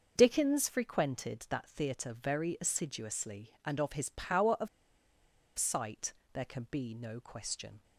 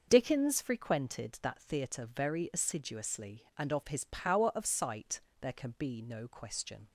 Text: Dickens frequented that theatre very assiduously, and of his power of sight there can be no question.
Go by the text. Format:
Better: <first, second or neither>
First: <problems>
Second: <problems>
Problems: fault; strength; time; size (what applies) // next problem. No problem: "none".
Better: second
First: starts louder than the rest; until 1.1 s; 6 dB // pauses between "of" and "sight"; noticeable; at 4.6 s; 0.90 s long // pauses between "sight" and "there"; slight; at 6.1 s; 0.18 s long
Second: starts louder than the rest; noticeable; until 1.1 s; 6 dB // pauses between "sight" and "there"; slight; at 5.2 s; 0.18 s long